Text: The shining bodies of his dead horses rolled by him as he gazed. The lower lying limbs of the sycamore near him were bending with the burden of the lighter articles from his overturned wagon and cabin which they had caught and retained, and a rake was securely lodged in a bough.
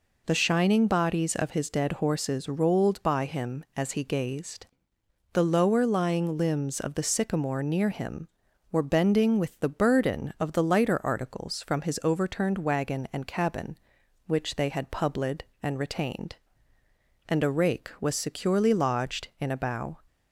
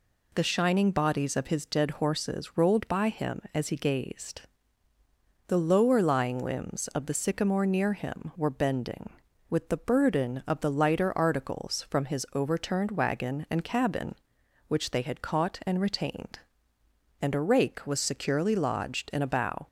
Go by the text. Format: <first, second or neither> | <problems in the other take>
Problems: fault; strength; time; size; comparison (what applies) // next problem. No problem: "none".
second | says "publid" for "caught"; at 14.9 s